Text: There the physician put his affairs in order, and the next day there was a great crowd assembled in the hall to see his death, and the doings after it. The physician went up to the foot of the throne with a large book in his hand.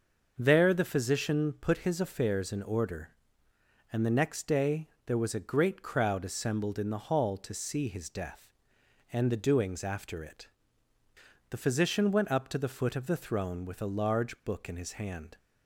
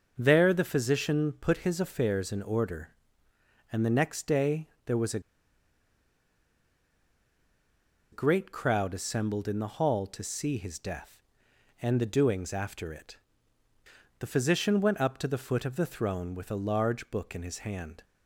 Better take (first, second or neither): first